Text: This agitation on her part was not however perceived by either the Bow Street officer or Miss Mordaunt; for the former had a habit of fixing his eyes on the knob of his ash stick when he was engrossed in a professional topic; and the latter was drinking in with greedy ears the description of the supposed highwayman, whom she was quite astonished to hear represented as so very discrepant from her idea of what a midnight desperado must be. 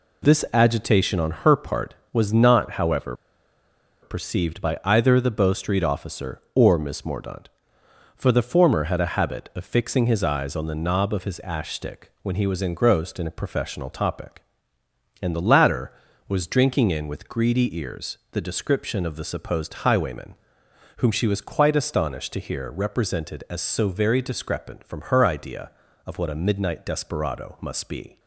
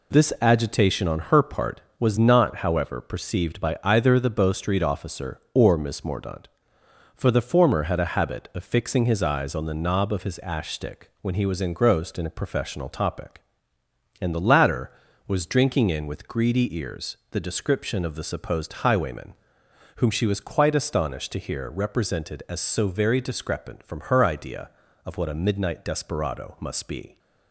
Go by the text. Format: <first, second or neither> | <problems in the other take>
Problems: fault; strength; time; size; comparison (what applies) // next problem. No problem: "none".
second | pauses between "however" and "perceived"; noticeable; at 3.1 s; 0.88 s long